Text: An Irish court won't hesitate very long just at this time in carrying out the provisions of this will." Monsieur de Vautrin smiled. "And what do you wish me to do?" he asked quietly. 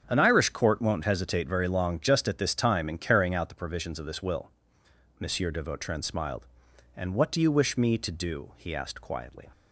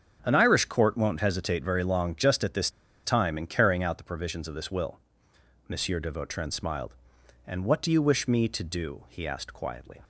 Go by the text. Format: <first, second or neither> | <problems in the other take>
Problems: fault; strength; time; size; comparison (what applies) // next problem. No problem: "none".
first | starts louder than the rest; strong; until 1.2 s; 7 dB; also in the first // pauses between "this" and "time"; slight; at 2.6 s; 0.35 s long